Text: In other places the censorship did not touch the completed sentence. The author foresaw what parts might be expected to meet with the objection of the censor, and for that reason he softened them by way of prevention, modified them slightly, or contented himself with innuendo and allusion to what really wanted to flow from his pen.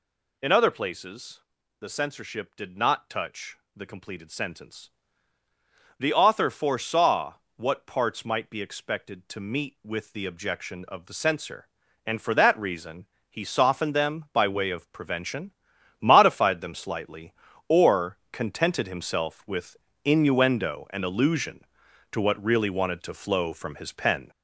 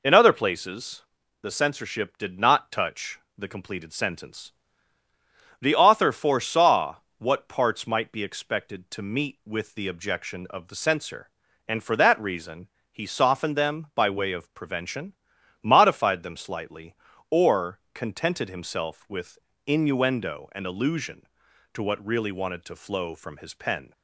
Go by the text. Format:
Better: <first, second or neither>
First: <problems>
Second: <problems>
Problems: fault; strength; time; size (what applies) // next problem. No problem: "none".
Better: second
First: gets louder; noticeable; throughout; 6 dB // pauses between "places" and "the"; at 1.4 s; 0.40 s long // pauses between "touch" and "the"; slight; at 3.5 s; 0.20 s long // pauses between "foresaw" and "what"; slight; at 7.3 s; 0.22 s long // pauses between "reason" and "he"; slight; at 13.0 s; 0.22 s long // pauses between "or" and "contented"; slight; at 18.1 s; 0.16 s long // pauses between "with" and "innuendo"; slight; at 19.7 s; 0.28 s long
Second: pauses between "places" and "the"; at 1.0 s; 0.40 s long // pauses between "touch" and "the"; slight; at 3.1 s; 0.20 s long // pauses between "foresaw" and "what"; slight; at 6.9 s; 0.22 s long // pauses between "reason" and "he"; slight; at 12.6 s; 0.22 s long // pauses between "or" and "contented"; slight; at 17.7 s; 0.16 s long // pauses between "with" and "innuendo"; slight; at 19.3 s; 0.28 s long